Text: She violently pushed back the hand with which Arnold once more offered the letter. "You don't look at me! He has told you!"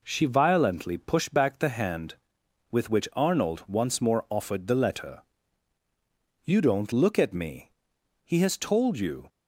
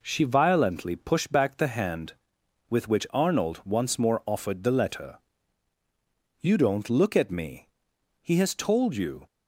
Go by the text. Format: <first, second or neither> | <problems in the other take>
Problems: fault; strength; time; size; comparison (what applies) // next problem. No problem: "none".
neither | none